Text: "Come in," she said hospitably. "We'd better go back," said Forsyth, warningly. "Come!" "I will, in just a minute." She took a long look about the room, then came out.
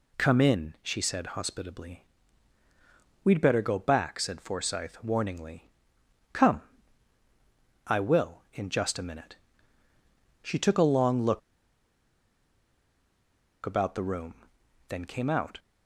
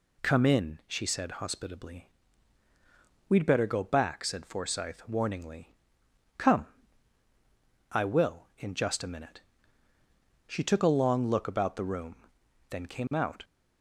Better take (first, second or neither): second